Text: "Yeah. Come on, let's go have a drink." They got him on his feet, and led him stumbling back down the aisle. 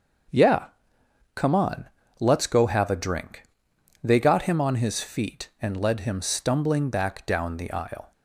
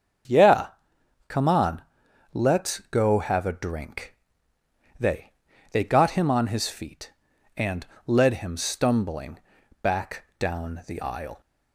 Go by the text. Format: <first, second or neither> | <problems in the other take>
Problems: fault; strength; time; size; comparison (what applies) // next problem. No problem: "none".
first | starts louder than the rest; until 2.3 s; 7 dB; strong in the first // says "They" twice; at 5.7 s // pauses between "and" and "led"; slight; at 7.8 s; 0.22 s long // pauses between "stumbling" and "back"; at 9.3 s; 0.44 s long // pauses between "back" and "down"; slight; at 10.2 s; 0.16 s long